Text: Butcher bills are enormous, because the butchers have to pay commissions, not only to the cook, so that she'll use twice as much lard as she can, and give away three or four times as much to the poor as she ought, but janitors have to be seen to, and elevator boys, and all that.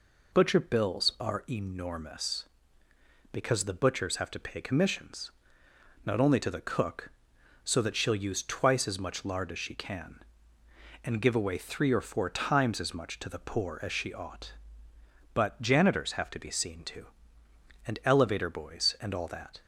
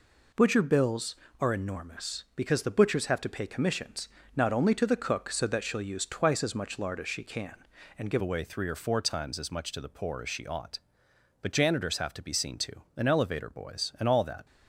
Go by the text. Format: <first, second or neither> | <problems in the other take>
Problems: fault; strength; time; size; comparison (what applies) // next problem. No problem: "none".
first | changes voice at "away"; from 8.2 s on; 6.2 s long